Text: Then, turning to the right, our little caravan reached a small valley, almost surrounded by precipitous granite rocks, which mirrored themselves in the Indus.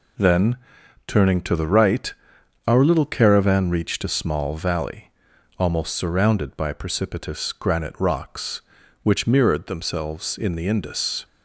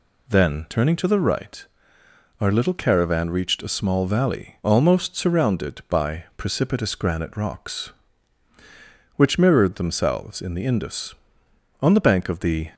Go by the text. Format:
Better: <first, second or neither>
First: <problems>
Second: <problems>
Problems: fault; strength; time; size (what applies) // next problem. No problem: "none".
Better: first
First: none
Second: goes on to say "On the bank of the"; noticeable; from 11.8 s on; 0.92 s long